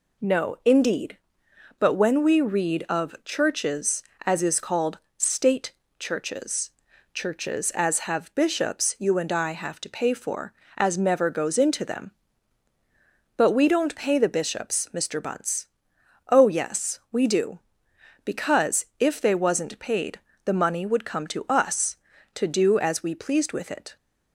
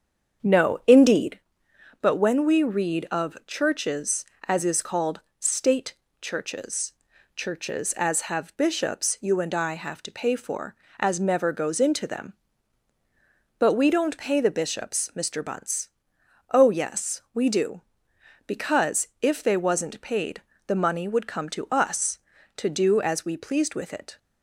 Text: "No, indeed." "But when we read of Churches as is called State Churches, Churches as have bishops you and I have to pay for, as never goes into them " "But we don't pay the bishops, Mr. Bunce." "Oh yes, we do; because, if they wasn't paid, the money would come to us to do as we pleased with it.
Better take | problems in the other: first | starts louder than the rest; strong; until 1.4 s; 7.5 dB // pauses between "called" and "State"; slight; at 5.1 s; 0.20 s long; slight in the first // pauses between "State" and "Churches"; slight; at 5.9 s; 0.26 s long; slight in the first

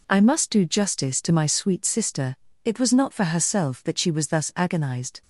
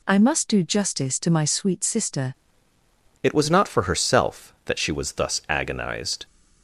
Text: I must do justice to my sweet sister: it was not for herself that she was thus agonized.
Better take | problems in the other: first | changes voice at "it"; from 3.2 s on; 3.0 s long

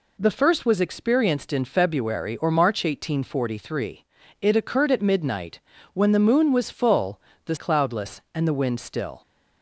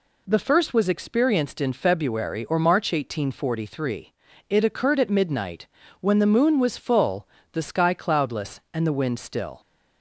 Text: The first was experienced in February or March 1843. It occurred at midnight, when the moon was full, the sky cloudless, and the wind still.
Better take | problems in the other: second | skips "sky"; at 7.5 s

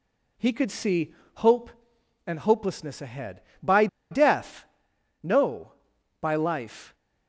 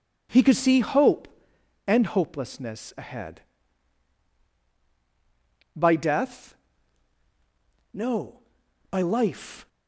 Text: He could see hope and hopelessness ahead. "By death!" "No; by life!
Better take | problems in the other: second | pauses between "see" and "hope"; slight; at 1.1 s; 0.20 s long // pauses between "By" and "death"; slight; at 3.8 s; 0.24 s long

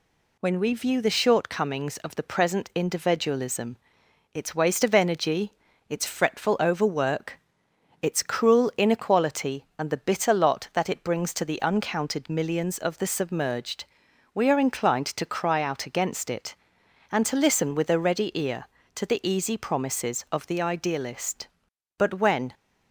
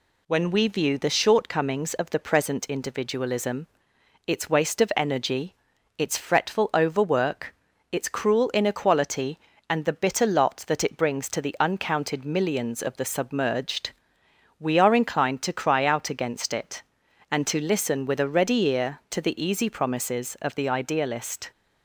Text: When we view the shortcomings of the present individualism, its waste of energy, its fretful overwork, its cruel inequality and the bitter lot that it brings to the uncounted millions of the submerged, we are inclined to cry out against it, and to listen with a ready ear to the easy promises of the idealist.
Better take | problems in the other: second | goes on to say "But when"; from 21.9 s on; 0.56 s long

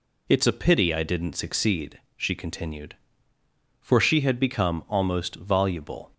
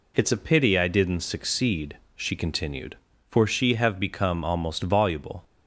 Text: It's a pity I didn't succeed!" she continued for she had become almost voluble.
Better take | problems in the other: first | says "have" for "had"; at 3.7 s

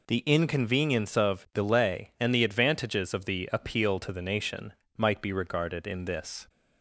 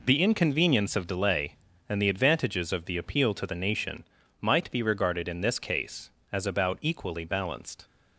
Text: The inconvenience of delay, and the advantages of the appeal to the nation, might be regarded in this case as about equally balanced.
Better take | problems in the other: second | stops before "case as about equally balanced"; at 6.4 s

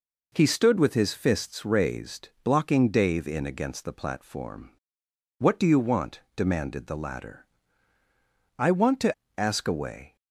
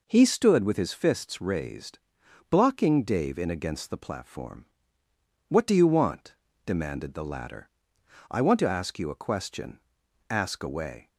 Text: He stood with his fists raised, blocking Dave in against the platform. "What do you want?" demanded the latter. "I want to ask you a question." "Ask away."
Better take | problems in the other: second | skips "ask you a question"; at 9.2 s

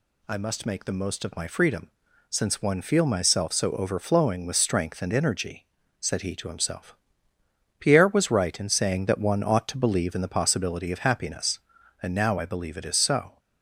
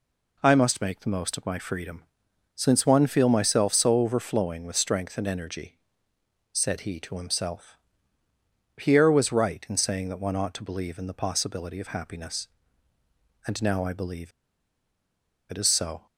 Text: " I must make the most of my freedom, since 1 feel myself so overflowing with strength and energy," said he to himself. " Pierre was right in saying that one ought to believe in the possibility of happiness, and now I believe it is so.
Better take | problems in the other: first | pauses between "believe" and "it"; at 14.3 s; 1.1 s long

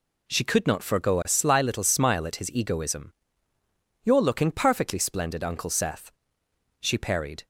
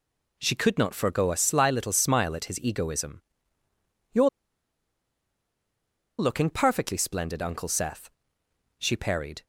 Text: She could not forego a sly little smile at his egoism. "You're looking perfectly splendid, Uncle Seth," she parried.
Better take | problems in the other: first | pauses between "You're" and "looking"; strong; at 4.2 s; 1.9 s long

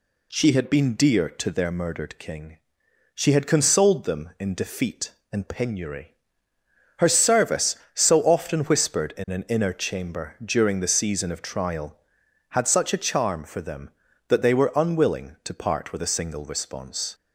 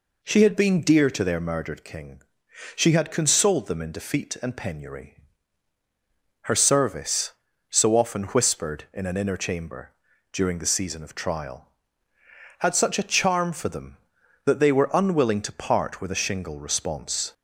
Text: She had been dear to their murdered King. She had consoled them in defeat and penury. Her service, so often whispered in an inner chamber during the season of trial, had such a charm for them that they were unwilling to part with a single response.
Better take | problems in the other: first | pauses between "chamber" and "during"; at 9.9 s; 0.42 s long // says "shingle" for "single"; at 16.1 s

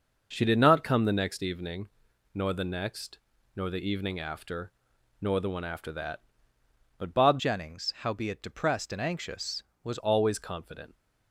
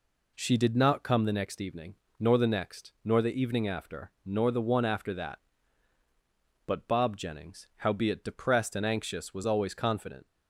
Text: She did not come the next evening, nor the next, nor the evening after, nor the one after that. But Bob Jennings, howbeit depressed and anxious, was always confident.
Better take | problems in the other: second | changes voice from "Jennings" to "was"; from 7.3 to 9.9 s; 2.6 s long

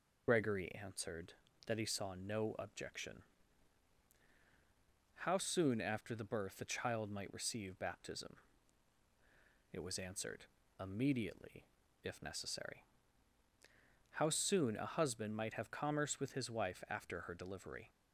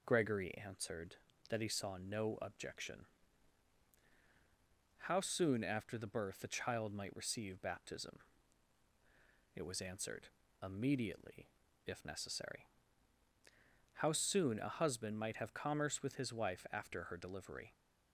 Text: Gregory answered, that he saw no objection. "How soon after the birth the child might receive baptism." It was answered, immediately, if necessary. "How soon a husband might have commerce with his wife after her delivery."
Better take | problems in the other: second | loses the start of "Gregory"; at 0.2 s; 50 ms

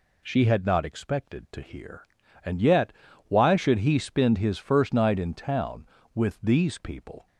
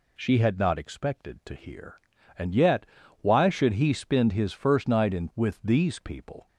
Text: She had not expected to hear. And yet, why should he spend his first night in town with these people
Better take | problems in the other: first | skips "town"; at 5.3 s

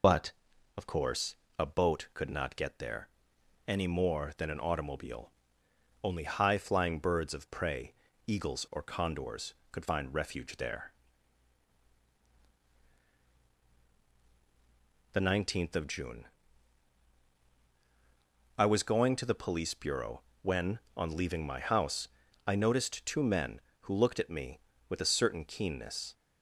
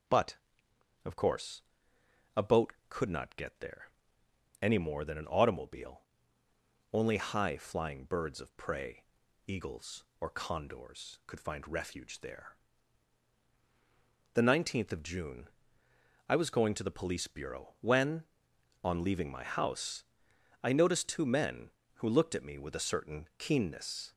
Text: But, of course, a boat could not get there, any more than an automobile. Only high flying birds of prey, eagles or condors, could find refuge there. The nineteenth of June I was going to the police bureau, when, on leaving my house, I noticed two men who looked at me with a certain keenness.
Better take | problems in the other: second | loses the start of "But"; at 0.0 s; 30 ms // pauses between "June" and "I"; strong; at 16.2 s; 2.3 s long; noticeable in the second

